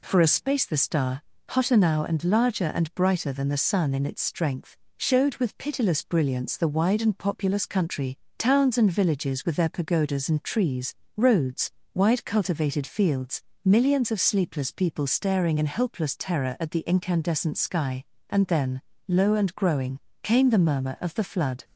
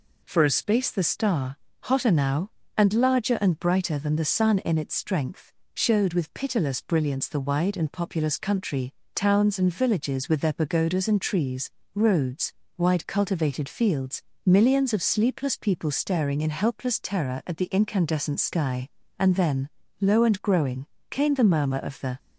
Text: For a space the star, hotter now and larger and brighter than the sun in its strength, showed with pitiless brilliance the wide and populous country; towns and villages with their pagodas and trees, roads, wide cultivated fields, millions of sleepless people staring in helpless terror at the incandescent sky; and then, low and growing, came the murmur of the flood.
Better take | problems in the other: first | stops before "flood"; at 22.1 s

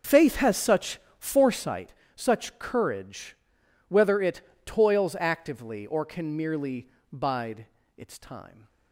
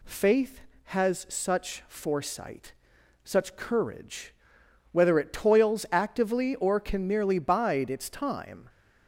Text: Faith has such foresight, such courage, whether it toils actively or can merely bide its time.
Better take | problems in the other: second | starts louder than the rest; noticeable; until 1.7 s; 6 dB // pauses between "such" and "foresight"; slight; at 0.9 s; 0.18 s long // pauses between "it" and "toils"; slight; at 4.3 s; 0.24 s long // pauses between "merely" and "bide"; slight; at 6.8 s; 0.24 s long // pauses between "bide" and "its"; slight; at 7.6 s; 0.32 s long

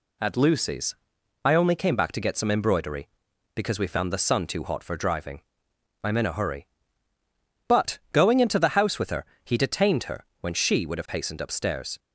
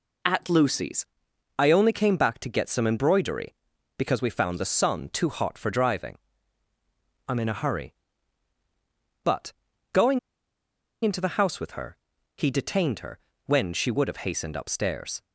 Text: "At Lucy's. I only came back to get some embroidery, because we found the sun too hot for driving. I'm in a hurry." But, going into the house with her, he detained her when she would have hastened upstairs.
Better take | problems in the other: first | pauses between "going" and "into"; noticeable; at 10.1 s; 0.84 s long // pauses between "her" and "when"; slight; at 13.1 s; 0.26 s long; slight in the first

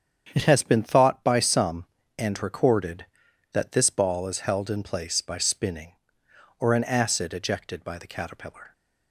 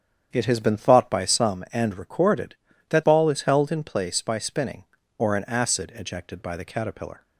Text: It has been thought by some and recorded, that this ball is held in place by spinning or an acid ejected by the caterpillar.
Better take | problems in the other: first | starts louder than the rest; strong; until 1.3 s; 8.5 dB; strong in the first // skips "this"; at 3.0 s

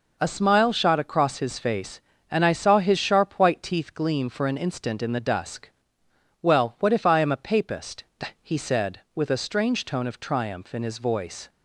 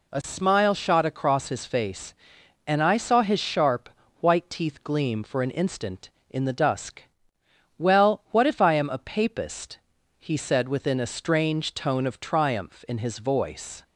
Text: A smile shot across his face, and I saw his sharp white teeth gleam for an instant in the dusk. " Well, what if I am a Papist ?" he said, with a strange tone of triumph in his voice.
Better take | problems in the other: first | pauses between "sharp" and "white"; slight; at 3.8 s; 0.30 s long // says "within" for "with"; at 10.6 s

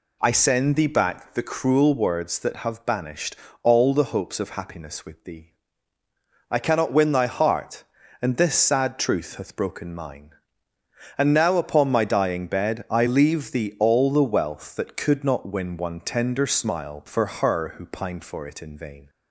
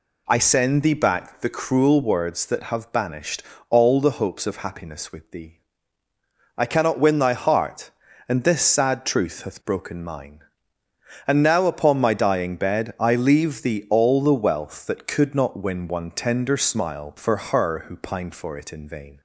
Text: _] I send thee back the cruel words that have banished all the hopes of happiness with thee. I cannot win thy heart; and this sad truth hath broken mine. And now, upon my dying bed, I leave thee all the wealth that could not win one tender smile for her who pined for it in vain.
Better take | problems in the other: neither | pauses between "banished" and "all"; slight; the same in both

